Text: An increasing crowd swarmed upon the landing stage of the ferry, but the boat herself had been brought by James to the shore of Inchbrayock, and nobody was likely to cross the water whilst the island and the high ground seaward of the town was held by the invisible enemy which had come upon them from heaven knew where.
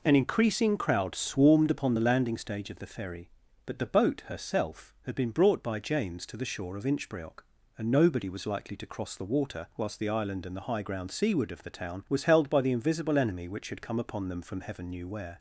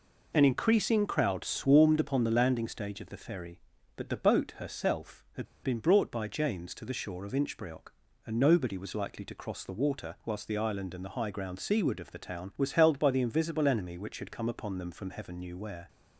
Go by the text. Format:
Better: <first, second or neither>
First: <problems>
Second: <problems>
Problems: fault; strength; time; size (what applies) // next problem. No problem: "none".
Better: first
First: none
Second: pauses between "had" and "been"; slight; at 5.4 s; 0.18 s long